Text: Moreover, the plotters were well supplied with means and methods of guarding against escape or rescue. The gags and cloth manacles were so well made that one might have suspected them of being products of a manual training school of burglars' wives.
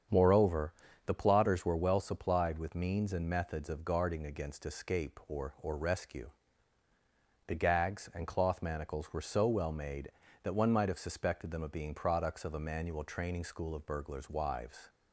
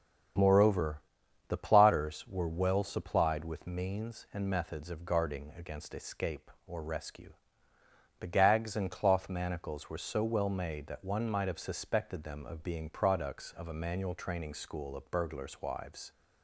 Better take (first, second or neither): second